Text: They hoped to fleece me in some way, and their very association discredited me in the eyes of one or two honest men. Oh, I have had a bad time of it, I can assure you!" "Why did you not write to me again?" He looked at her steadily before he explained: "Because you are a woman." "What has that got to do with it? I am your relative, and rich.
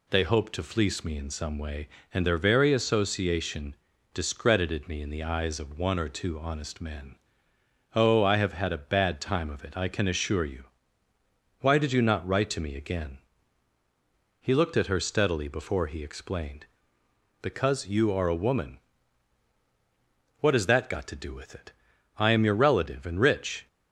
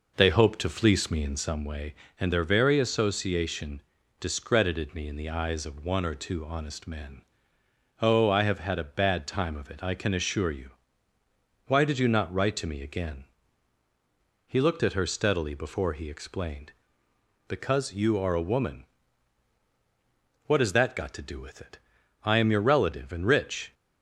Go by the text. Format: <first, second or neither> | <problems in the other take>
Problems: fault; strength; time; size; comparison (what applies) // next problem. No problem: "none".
first | starts louder than the rest; noticeable; until 1.7 s; 5 dB // pauses between "association" and "discredited"; at 3.8 s; 0.38 s long; also in the first